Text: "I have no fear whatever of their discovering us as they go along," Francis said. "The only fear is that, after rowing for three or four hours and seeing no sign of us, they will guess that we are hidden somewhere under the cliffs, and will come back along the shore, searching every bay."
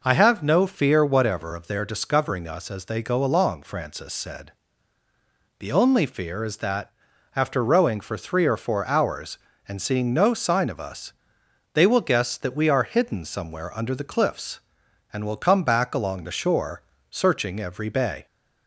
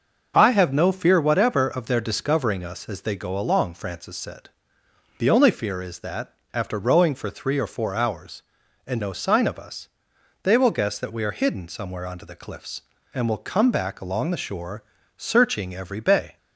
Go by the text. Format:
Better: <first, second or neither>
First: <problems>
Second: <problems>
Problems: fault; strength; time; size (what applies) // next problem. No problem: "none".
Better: first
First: none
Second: starts louder than the rest; until 1.3 s; 6.5 dB // skips "seeing"; at 9.0 s